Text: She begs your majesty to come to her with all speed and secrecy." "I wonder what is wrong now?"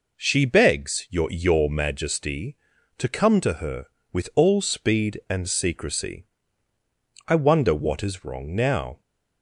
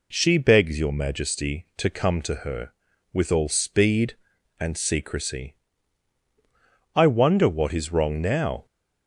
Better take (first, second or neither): second